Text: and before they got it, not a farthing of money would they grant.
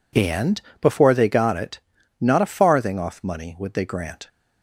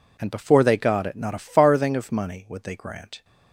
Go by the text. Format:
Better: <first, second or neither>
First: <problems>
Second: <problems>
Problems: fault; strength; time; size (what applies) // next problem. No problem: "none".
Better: second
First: pauses between "and" and "before"; slight; at 0.5 s; 0.20 s long // says "off" for "of"; at 2.9 s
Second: none